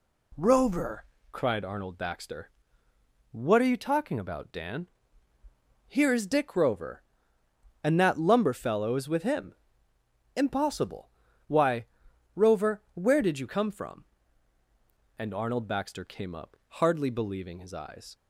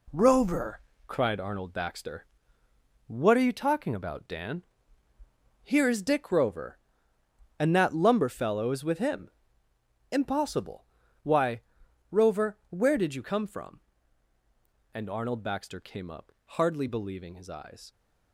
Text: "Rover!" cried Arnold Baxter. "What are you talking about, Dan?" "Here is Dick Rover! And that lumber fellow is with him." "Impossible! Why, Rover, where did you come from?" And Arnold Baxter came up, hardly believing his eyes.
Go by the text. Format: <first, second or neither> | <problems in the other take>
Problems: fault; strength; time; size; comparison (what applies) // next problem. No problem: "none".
first | gets quieter; strong; throughout; 7.5 dB